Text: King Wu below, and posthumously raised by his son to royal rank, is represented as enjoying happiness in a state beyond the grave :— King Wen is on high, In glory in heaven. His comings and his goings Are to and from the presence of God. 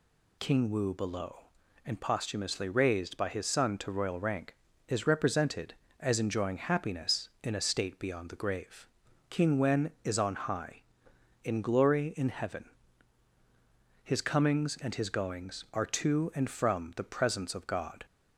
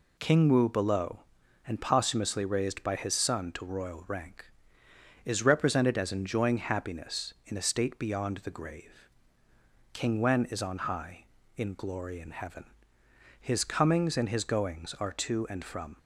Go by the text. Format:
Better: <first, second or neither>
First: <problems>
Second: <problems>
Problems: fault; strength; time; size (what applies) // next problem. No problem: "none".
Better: first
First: none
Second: stops before "the presence of God"; at 15.9 s